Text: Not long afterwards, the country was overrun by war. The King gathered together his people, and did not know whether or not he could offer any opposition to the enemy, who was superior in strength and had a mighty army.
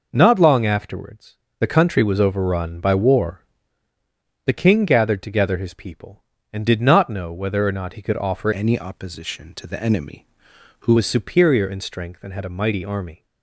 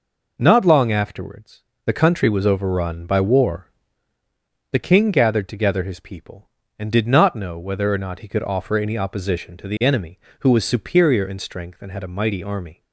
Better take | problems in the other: second | changes voice from "any" to "who"; from 8.5 to 10.9 s; 2.4 s long

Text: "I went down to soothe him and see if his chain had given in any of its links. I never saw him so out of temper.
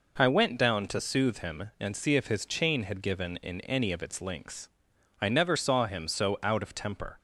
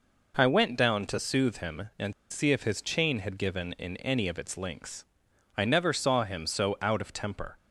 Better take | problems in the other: first | pauses between "and" and "see"; slight; at 2.1 s; 0.17 s long

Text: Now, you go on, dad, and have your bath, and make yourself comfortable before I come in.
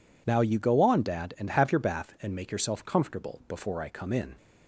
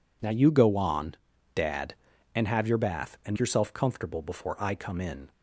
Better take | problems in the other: first | skips "make"; at 3.3 s

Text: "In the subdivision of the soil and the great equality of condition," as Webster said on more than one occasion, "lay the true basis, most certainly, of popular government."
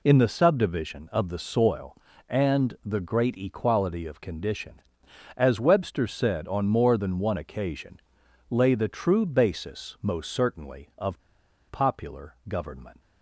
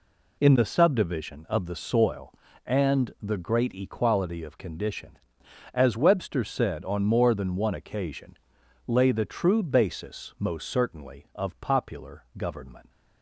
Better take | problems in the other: second | pauses between "of" and "popular"; noticeable; at 11.2 s; 0.48 s long

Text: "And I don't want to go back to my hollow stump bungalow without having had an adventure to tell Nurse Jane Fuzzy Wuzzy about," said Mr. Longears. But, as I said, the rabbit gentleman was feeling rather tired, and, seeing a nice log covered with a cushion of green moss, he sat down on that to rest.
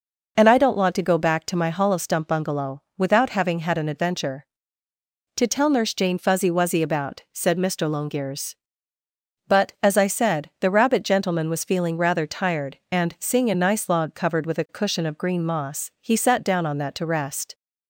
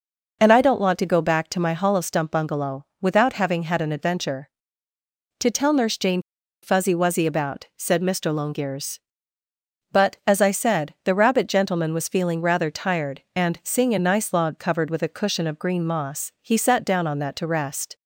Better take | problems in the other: first | pauses between "bungalow" and "without"; slight; at 2.8 s; 0.16 s long; slight in the first // pauses between "Jane" and "Fuzzy"; at 6.2 s; 0.41 s long

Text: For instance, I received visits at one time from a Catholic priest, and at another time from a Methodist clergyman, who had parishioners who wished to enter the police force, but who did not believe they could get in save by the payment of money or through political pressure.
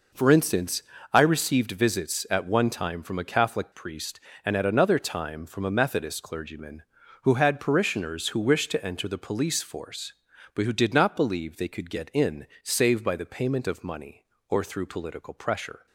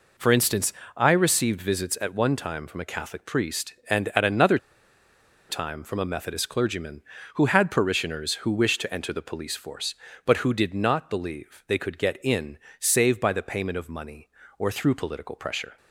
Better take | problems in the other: first | pauses between "another" and "time"; noticeable; at 4.5 s; 0.91 s long // pauses between "in" and "save"; slight; at 12.5 s; 0.22 s long; slight in the first

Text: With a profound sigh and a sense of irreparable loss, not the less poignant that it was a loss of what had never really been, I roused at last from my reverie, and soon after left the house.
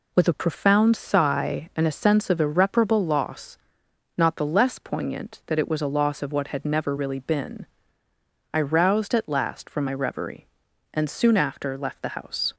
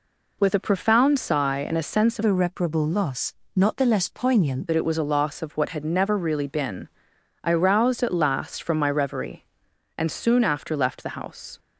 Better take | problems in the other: first | changes voice from "irreparable" to "poignant"; from 2.2 to 4.6 s; 2.4 s long

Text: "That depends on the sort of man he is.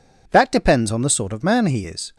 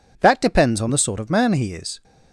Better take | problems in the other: neither | none

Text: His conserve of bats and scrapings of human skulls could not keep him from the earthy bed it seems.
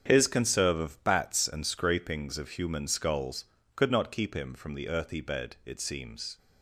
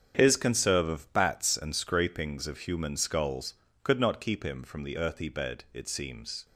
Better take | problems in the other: neither | starts louder than the rest; the same in both

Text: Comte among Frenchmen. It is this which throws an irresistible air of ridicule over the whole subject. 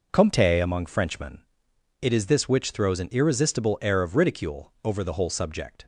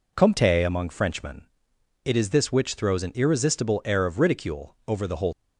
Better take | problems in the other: first | stops before "subject"; at 5.3 s

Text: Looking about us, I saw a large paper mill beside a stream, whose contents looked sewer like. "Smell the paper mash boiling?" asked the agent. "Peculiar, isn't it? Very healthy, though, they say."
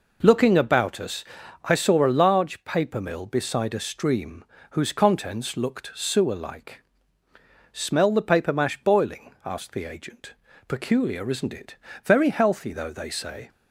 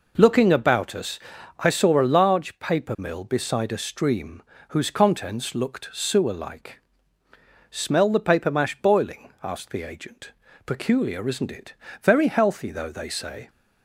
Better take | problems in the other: neither | none

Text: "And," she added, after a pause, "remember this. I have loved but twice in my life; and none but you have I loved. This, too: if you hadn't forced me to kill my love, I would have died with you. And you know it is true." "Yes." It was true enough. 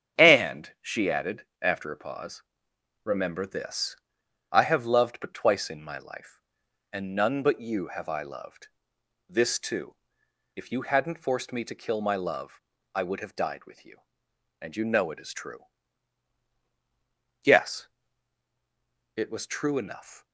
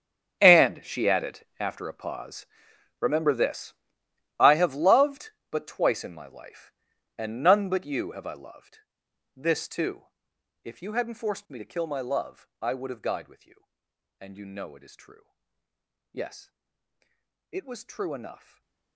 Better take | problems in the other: first | gets quieter; strong; throughout; 16 dB // starts louder than the rest; strong; until 1.4 s; 7.5 dB; strong in the first // stays silent after the last word; slight; from 18.3 s on; 0.6 s long

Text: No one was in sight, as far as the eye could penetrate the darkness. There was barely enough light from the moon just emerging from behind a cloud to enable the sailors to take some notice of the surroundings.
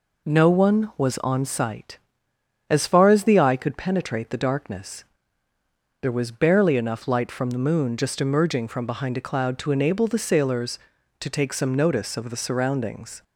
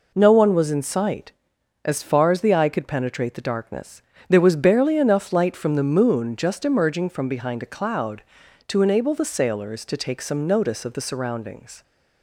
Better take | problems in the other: second | says "on" for "in"; at 1.1 s

